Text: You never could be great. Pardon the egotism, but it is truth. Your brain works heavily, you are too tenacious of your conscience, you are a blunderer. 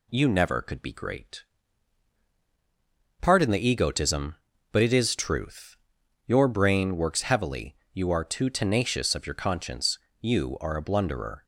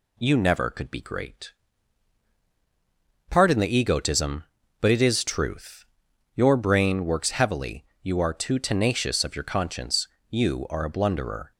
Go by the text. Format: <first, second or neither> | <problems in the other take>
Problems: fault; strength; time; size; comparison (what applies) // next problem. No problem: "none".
neither | none